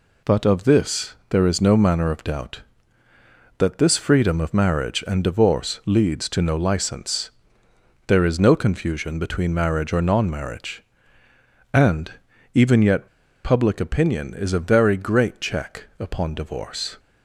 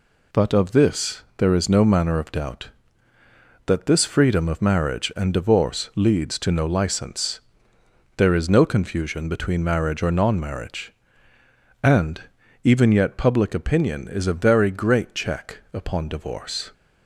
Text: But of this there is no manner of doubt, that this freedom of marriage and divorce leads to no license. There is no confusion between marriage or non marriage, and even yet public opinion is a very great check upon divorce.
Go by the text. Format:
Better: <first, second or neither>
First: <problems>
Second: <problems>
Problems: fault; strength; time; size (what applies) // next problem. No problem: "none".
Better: second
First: pauses between "and" and "even"; at 12.1 s; 0.42 s long // pauses between "yet" and "public"; at 13.0 s; 0.37 s long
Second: pauses between "and" and "even"; at 12.2 s; 0.42 s long